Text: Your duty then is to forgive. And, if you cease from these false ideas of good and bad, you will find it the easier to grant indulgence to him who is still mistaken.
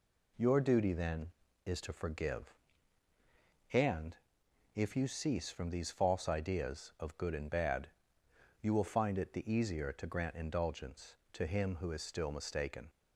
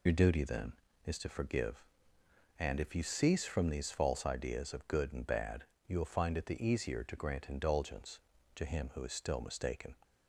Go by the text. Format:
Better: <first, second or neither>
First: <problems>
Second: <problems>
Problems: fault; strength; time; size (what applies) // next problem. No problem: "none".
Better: first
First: none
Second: loses the start of "Your"; at 0.0 s; 45 ms